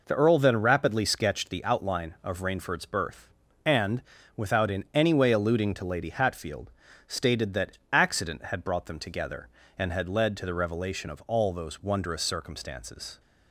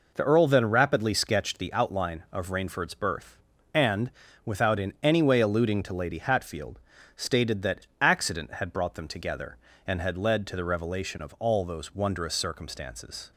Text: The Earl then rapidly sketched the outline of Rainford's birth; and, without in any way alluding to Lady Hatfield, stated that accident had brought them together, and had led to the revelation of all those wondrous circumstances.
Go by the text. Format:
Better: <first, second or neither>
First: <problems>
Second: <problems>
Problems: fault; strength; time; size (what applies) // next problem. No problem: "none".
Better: neither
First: none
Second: none